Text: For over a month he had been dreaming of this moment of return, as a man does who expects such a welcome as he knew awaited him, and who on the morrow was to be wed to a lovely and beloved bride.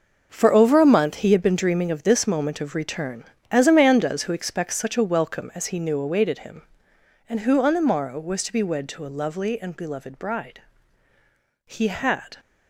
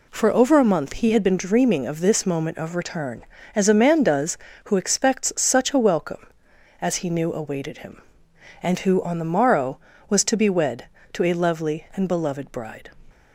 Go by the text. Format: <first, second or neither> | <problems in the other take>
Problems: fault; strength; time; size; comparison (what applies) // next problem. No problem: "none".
second | goes on to say "He had"; noticeable; from 11.6 s on; 0.70 s long